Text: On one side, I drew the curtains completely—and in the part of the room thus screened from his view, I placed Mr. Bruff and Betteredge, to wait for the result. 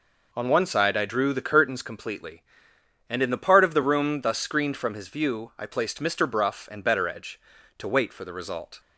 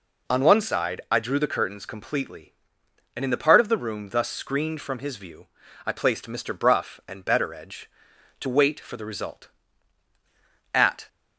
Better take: first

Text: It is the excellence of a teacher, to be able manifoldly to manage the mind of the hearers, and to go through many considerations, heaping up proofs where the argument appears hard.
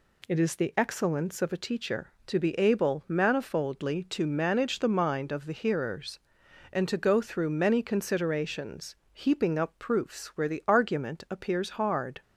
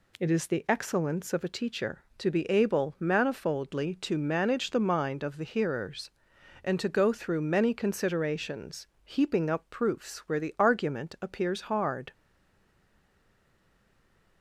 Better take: first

